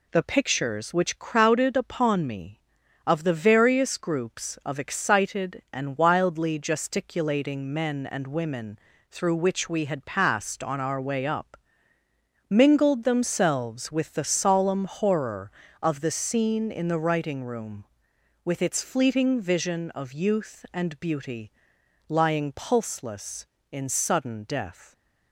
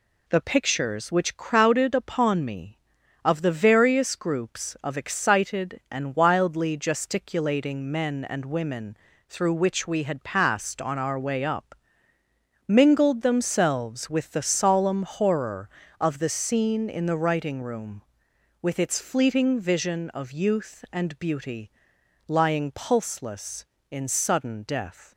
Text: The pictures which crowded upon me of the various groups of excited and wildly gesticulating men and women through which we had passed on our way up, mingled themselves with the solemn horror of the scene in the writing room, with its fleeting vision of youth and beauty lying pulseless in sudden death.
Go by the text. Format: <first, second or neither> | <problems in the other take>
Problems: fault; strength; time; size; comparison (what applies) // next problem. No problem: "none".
neither | pauses between "women" and "through"; slight; the same in both // pauses between "beauty" and "lying"; noticeable; the same in both